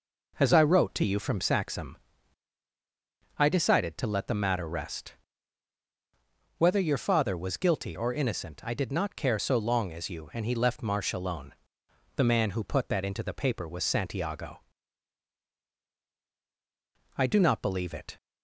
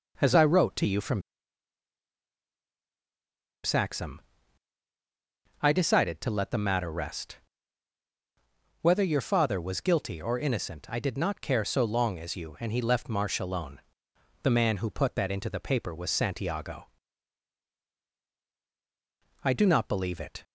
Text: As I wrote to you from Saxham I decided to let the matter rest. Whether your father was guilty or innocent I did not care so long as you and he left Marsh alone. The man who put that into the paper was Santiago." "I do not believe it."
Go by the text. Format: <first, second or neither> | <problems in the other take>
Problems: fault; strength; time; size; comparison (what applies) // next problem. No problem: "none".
first | pauses between "from" and "Saxham"; strong; at 1.2 s; 2.4 s long // pauses between "Saxham" and "I"; strong; at 4.2 s; 1.4 s long; strong in the first